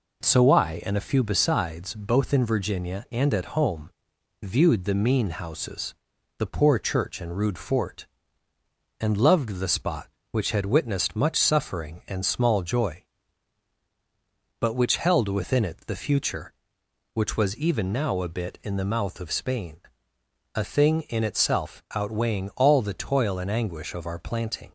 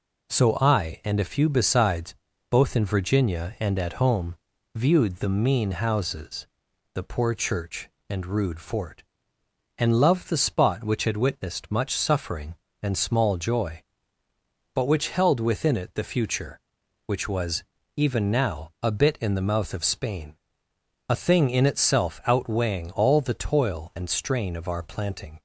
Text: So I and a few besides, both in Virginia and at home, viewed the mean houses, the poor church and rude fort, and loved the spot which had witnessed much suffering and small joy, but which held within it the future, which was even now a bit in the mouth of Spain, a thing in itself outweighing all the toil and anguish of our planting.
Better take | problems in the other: first | pauses between "was" and "even"; slight; at 17.6 s; 0.32 s long // says "strain" for "anguish"; at 24.0 s

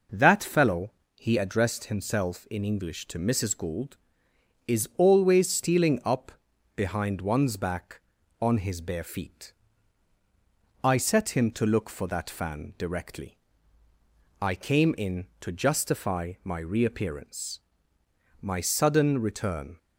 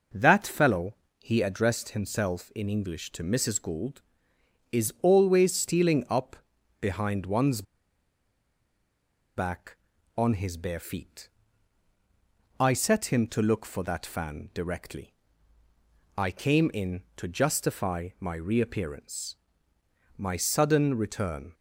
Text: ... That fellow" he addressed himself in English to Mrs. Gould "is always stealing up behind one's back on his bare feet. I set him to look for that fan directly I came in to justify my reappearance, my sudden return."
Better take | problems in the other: first | pauses between "fellow" and "he"; slight; at 0.9 s; 0.24 s long; slight in the first // pauses between "up" and "behind"; noticeable; at 6.3 s; 0.46 s long; noticeable in the first // pauses between "one's" and "back"; strong; at 7.6 s; 1.7 s long // pauses between "directly" and "I"; at 15.1 s; 1.0 s long; also in the first

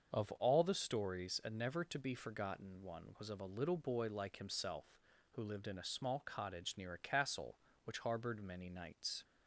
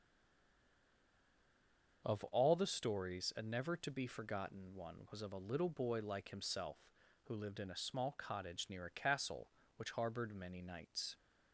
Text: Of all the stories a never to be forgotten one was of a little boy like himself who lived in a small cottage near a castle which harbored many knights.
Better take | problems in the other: first | stays silent before the first word; noticeable; until 2.0 s; 2.0 s long // starts louder than the rest; until 3.0 s; 6.5 dB; also in the first

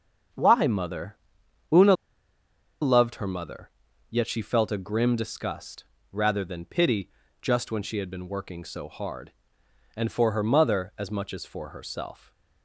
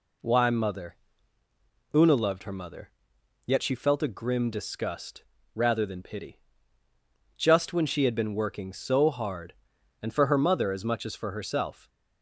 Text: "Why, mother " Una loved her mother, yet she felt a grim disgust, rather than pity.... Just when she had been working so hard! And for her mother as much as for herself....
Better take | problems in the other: second | pauses between "Una" and "loved"; noticeable; at 1.9 s; 0.88 s long // stays silent after the last word; slight; from 12.1 s on; 0.5 s long

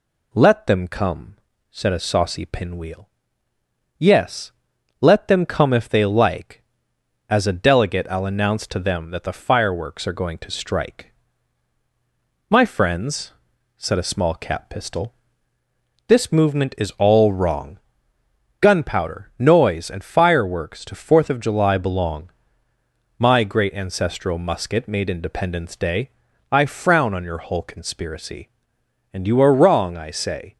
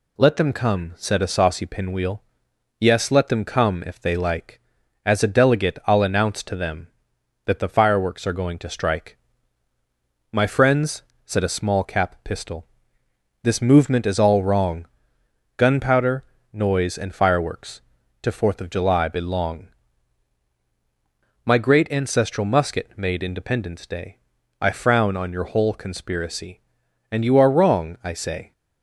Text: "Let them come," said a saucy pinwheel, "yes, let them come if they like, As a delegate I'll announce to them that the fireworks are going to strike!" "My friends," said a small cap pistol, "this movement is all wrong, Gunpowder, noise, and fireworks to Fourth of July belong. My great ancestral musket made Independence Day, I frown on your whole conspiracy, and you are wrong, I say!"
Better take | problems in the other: neither | none

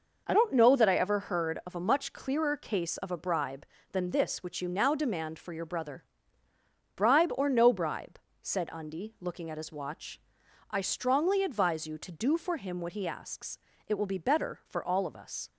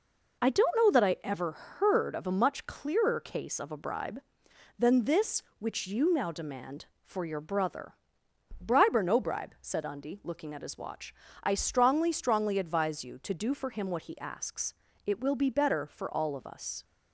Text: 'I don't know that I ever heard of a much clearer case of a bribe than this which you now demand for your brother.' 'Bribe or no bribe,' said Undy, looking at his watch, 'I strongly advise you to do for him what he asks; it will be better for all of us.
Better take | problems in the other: first | says "strongly" twice; at 12.1 s

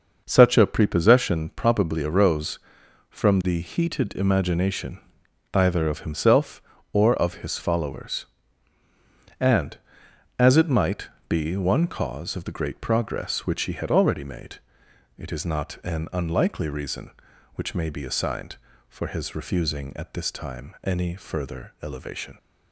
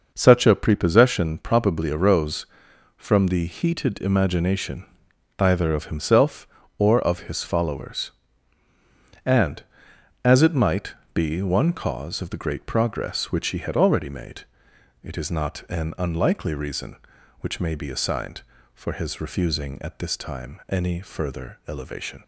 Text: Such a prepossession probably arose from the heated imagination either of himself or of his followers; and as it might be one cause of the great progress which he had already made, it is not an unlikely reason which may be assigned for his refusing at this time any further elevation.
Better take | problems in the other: neither | pauses between "imagination" and "either"; noticeable; the same in both // pauses between "might" and "be"; slight; the same in both

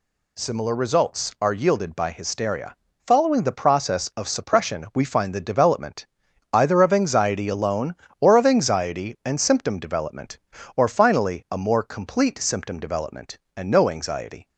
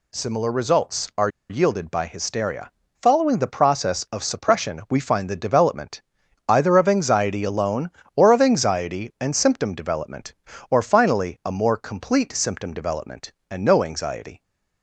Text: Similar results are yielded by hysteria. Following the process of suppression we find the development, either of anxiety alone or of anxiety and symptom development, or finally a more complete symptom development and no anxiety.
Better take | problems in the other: first | pauses between "are" and "yielded"; slight; at 1.2 s; 0.20 s long

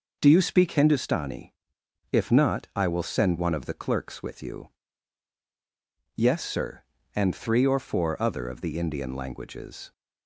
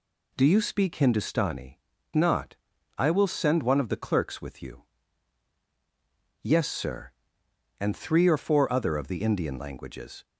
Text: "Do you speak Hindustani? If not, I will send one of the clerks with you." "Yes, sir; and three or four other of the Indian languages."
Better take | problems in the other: first | skips "If"; at 1.9 s

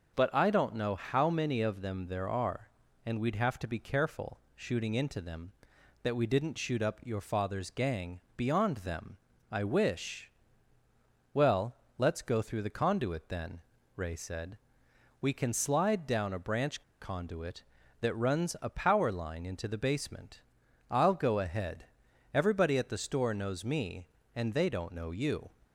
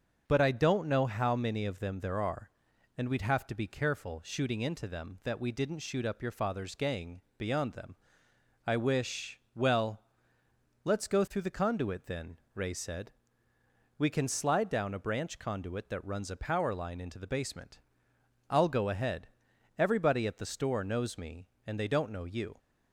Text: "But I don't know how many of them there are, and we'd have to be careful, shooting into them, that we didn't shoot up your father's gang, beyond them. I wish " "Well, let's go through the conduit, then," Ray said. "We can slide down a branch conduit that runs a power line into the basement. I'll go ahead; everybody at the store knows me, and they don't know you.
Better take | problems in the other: second | starts louder than the rest; until 1.1 s; 6 dB; also in the second // pauses between "branch" and "conduit"; slight; at 16.8 s; 0.17 s long

